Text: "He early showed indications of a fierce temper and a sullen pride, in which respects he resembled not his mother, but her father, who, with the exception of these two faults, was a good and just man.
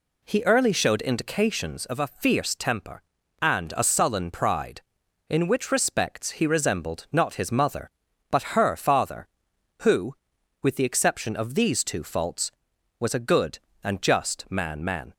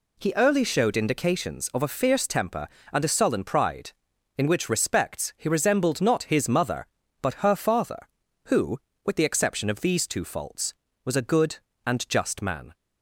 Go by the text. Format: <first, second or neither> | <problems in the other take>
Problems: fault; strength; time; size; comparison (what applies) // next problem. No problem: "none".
second | says "man" twice; at 14.8 s